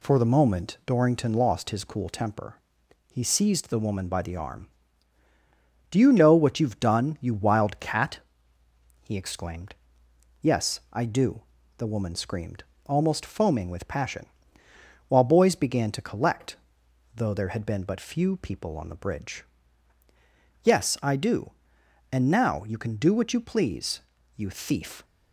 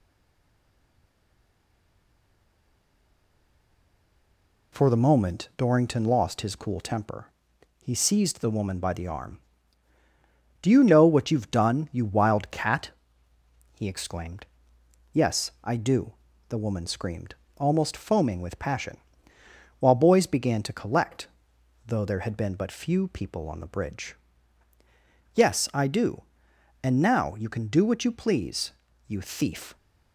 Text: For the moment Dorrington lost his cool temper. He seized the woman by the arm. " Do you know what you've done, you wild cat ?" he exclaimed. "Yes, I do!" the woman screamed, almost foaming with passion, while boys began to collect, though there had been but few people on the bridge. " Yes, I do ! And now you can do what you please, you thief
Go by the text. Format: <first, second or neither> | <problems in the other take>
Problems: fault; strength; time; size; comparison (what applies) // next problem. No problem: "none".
first | stays silent before the first word; strong; until 4.7 s; 4.7 s long